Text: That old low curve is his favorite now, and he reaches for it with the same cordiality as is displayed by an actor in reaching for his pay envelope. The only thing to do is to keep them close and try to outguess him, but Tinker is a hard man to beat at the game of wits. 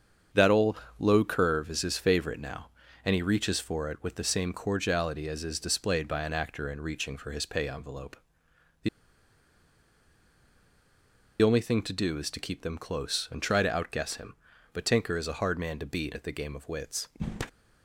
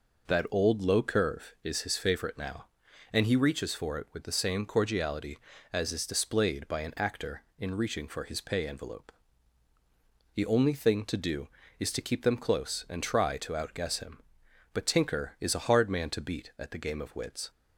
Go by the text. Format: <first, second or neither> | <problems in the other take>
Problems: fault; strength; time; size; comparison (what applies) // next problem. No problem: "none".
second | starts louder than the rest; strong; until 1.5 s; 7.5 dB // pauses between "old" and "low"; slight; at 0.7 s; 0.20 s long // pauses between "The" and "only"; strong; at 8.8 s; 2.5 s long